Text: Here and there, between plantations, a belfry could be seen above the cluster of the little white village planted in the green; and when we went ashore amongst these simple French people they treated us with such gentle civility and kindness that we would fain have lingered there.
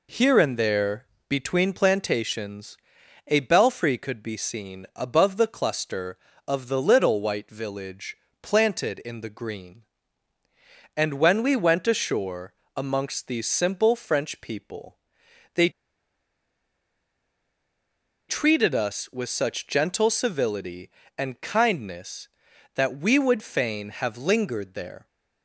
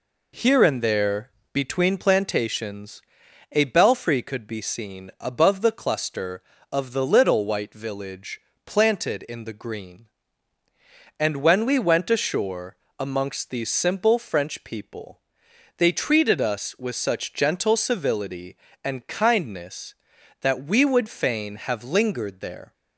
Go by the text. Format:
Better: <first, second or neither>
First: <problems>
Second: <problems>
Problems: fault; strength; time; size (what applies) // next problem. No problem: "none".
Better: second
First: pauses between "village" and "planted"; slight; at 8.1 s; 0.26 s long // pauses between "ashore" and "amongst"; slight; at 12.5 s; 0.22 s long // pauses between "people" and "they"; noticeable; at 14.9 s; 0.56 s long // pauses between "they" and "treated"; strong; at 15.6 s; 2.5 s long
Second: pauses between "village" and "planted"; slight; at 8.3 s; 0.26 s long // pauses between "ashore" and "amongst"; slight; at 12.7 s; 0.22 s long // pauses between "people" and "they"; noticeable; at 15.2 s; 0.56 s long